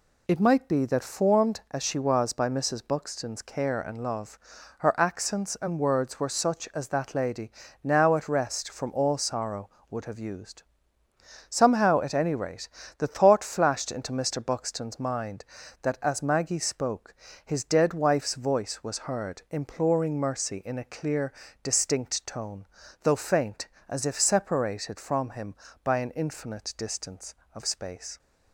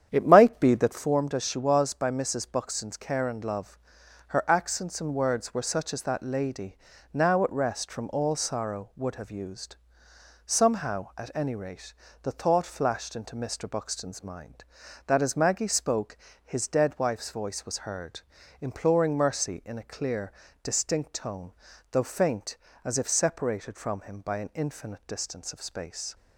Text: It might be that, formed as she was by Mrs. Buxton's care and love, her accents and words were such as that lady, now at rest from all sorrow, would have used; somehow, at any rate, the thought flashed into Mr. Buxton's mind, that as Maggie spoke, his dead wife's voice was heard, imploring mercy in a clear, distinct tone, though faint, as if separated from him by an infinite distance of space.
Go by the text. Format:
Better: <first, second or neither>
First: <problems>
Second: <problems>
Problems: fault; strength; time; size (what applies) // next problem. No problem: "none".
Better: first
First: none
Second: starts louder than the rest; strong; until 1.1 s; 9 dB